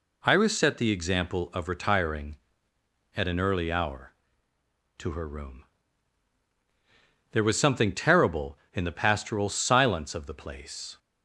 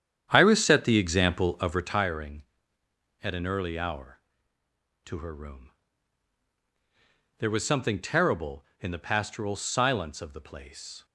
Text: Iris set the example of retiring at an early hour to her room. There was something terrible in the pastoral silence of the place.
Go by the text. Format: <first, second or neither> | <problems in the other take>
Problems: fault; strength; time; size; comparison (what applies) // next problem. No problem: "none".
first | starts louder than the rest; strong; until 2.1 s; 9 dB